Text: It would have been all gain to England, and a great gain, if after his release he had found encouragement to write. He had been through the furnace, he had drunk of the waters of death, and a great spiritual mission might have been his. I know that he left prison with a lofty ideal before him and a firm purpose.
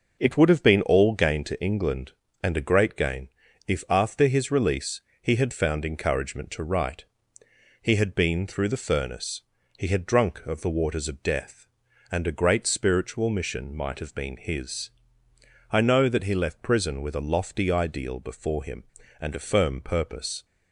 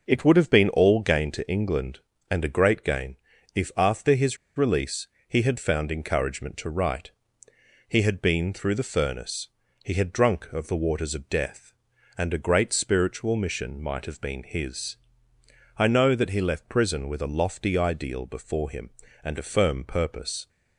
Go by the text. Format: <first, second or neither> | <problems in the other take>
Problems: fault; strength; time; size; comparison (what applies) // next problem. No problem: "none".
first | pauses between "his" and "release"; slight; at 4.3 s; 0.21 s long // pauses between "release" and "he"; slight; at 5.0 s; 0.20 s long; slight in the first